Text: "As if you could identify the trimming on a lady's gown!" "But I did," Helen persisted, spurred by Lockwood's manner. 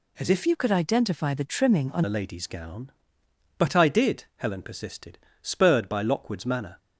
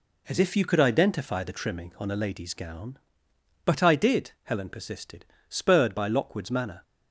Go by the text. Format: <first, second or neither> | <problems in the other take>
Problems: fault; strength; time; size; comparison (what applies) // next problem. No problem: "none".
second | changes voice from "you" to "on"; from 0.4 to 2.0 s; 1.6 s long